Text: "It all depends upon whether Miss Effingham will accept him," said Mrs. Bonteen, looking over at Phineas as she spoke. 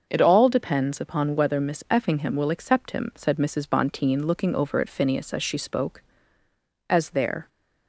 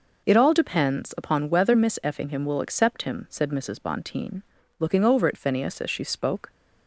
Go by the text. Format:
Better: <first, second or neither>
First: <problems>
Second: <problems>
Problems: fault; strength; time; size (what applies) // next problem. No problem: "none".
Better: second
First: starts louder than the rest; until 1.0 s; 6 dB // goes on to say "As there"; from 6.8 s on; 0.60 s long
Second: none